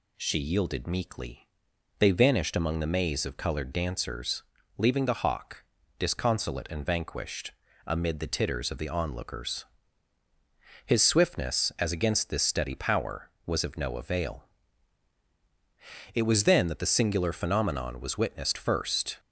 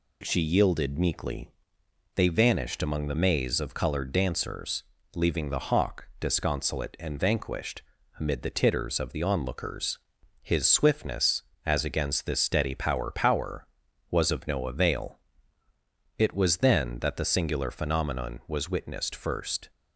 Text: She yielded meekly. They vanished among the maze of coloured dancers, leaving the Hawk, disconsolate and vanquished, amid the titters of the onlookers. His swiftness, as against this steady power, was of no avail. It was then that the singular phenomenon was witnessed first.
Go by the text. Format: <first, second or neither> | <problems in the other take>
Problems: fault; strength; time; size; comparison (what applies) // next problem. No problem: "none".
first | says "power" twice; at 13.0 s